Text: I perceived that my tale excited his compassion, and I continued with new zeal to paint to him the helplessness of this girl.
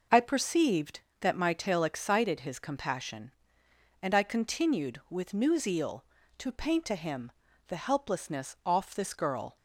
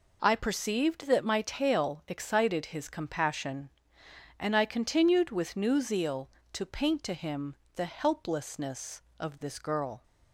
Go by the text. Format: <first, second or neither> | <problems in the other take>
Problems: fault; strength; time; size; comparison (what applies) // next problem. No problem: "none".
second | pauses between "him" and "the"; slight; at 7.3 s; 0.34 s long; slight in the second // says "off" for "of"; at 8.6 s